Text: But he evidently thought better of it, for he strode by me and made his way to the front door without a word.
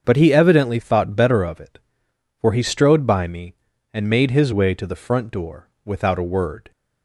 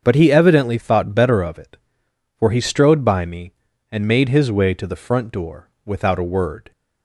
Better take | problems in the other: neither | starts louder than the rest; the same in both // pauses between "door" and "without"; slight; the same in both

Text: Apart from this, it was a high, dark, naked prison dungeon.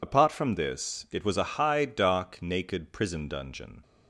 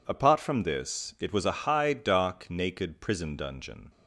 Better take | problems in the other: second | loses the start of "Apart"; at 0.0 s; 40 ms

